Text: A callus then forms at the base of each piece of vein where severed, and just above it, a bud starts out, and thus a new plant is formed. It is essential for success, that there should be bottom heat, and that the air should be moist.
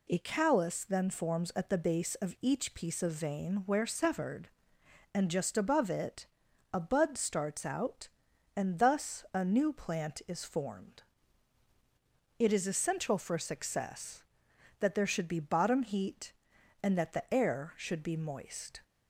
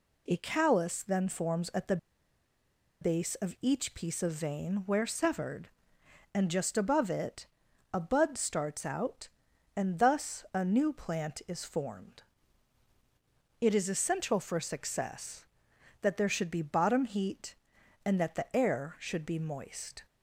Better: first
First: none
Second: pauses between "the" and "base"; at 1.9 s; 1.0 s long

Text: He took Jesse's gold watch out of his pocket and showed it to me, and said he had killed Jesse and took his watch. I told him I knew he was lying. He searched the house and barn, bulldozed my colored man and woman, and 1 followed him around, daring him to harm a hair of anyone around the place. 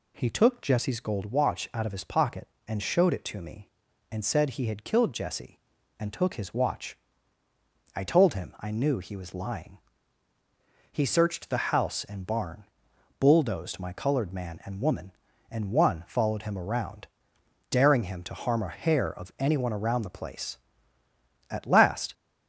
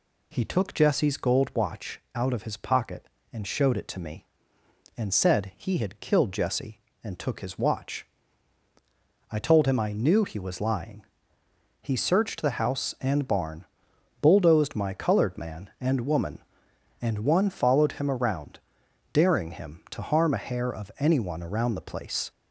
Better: second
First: goes on to say "At last"; noticeable; from 21.4 s on; 0.64 s long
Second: none

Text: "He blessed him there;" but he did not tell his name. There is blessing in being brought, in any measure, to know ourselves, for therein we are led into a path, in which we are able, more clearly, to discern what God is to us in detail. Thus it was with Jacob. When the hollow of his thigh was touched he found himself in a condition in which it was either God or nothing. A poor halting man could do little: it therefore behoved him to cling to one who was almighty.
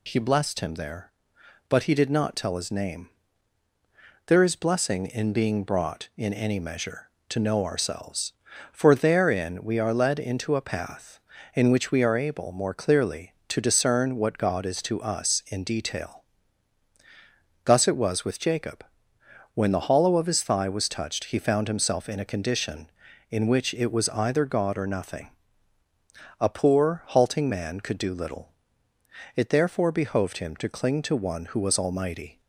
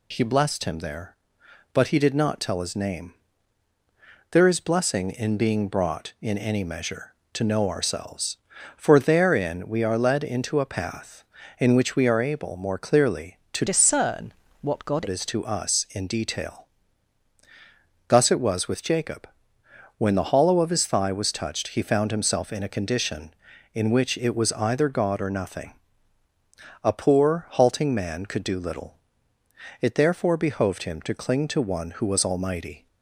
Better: first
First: none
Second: changes voice from "discern" to "God"; from 13.6 to 15.0 s; 1.4 s long // pauses between "discern" and "what"; slight; at 14.3 s; 0.28 s long

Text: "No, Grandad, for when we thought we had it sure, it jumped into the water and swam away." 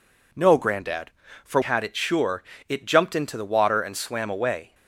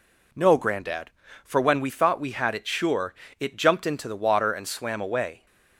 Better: second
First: skips "when we thought we"; at 1.6 s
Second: none

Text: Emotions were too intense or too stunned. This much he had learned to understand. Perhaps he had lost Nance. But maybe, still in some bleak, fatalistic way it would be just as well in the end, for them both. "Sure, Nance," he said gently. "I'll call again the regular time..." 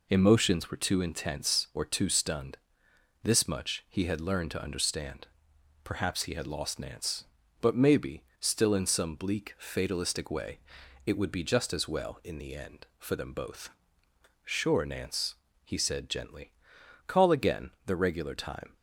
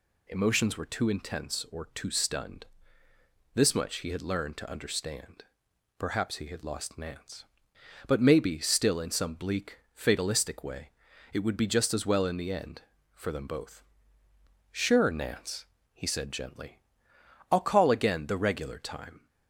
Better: second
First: pauses between "way" and "it"; noticeable; at 10.5 s; 0.46 s long // skips "I'll"; at 16.7 s // pauses between "again" and "the"; slight; at 17.6 s; 0.16 s long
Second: pauses between "way" and "it"; at 10.9 s; 0.42 s long

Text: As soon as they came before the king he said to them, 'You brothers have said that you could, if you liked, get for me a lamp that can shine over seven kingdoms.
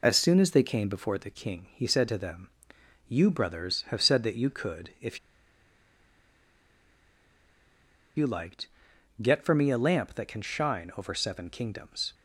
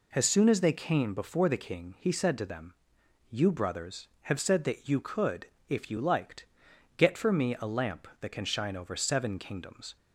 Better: second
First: pauses between "if" and "you"; strong; at 5.1 s; 2.9 s long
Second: none

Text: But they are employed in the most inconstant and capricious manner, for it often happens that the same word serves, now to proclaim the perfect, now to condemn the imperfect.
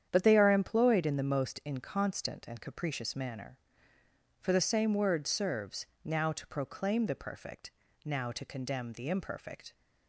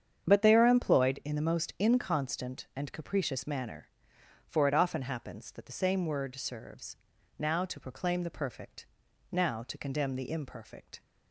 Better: second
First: starts louder than the rest; strong; until 1.1 s; 9 dB // skips "it often happens that"; at 4.5 s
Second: starts louder than the rest; strong; until 1.3 s; 8 dB

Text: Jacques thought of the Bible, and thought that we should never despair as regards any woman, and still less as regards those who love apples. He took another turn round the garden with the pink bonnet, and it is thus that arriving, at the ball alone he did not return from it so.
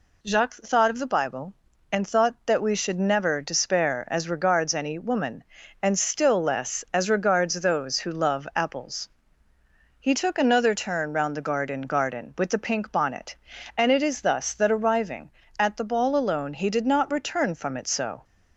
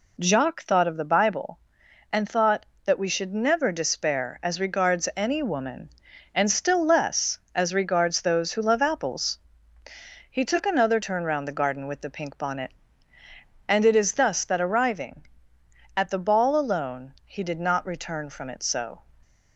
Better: second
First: says "garden" twice; at 11.7 s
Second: none

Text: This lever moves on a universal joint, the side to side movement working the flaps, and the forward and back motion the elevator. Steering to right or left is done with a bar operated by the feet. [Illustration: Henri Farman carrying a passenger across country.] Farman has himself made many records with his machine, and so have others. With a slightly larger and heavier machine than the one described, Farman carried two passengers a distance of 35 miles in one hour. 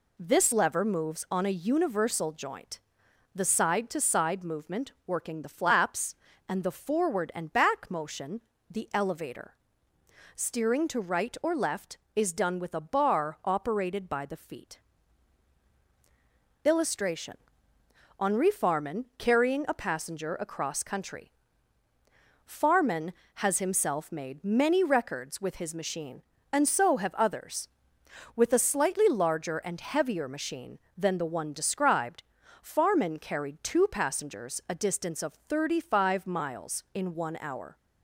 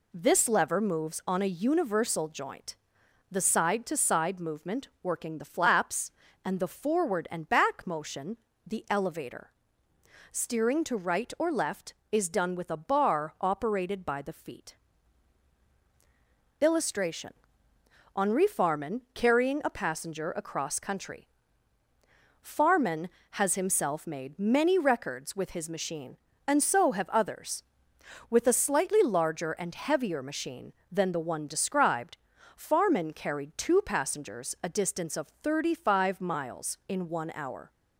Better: neither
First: pauses between "motion" and "the"; slight; at 8.4 s; 0.28 s long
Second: pauses between "motion" and "the"; slight; at 8.3 s; 0.28 s long

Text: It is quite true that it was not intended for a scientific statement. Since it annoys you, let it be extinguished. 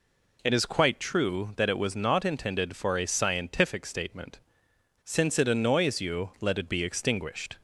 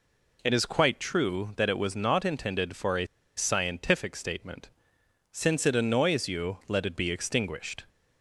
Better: first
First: none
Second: pauses between "a" and "scientific"; slight; at 3.0 s; 0.30 s long

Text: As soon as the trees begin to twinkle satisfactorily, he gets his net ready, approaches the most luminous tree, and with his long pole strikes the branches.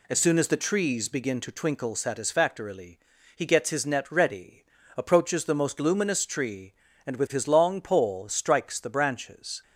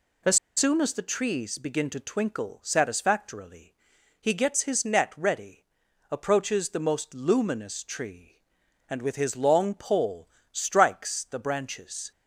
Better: first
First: none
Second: pauses between "As" and "soon"; slight; at 0.3 s; 0.20 s long // pauses between "pole" and "strikes"; slight; at 10.2 s; 0.24 s long

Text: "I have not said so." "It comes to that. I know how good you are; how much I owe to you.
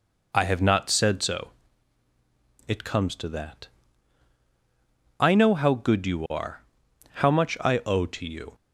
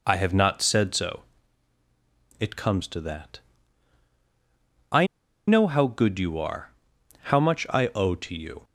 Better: first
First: none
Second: pauses between "I" and "know"; at 5.0 s; 0.41 s long

